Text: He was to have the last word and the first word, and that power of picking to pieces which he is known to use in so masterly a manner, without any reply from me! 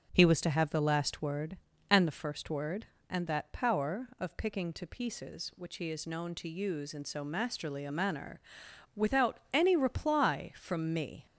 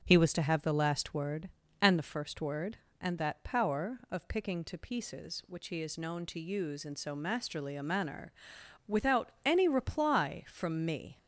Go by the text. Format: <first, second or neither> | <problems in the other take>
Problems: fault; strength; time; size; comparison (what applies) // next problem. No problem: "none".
neither | starts louder than the rest; the same in both